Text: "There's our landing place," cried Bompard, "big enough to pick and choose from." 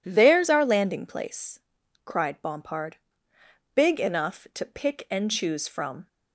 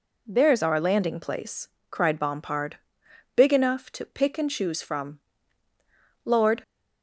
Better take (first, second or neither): first